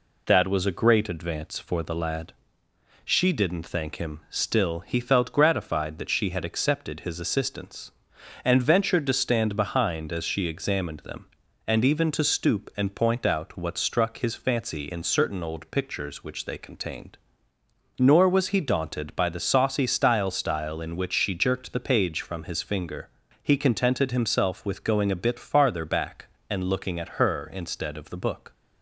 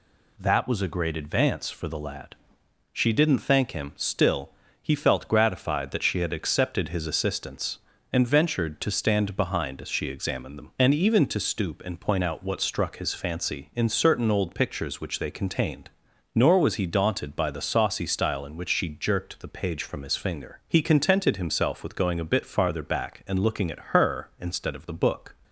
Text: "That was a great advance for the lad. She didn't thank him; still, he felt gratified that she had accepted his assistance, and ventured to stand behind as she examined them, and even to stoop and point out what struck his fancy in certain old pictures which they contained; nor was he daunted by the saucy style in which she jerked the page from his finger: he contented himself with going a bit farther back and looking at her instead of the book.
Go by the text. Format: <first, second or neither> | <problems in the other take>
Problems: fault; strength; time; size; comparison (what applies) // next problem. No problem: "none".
second | says "style" twice; at 20.3 s